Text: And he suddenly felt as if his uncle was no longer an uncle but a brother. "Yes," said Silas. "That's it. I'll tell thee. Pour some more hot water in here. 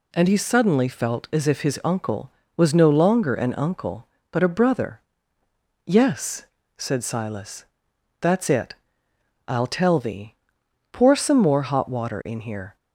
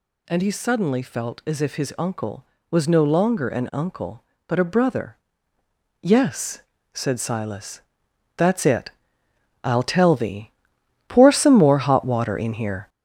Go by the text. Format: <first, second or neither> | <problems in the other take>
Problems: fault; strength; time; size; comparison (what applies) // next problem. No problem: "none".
first | gets louder; noticeable; throughout; 5.5 dB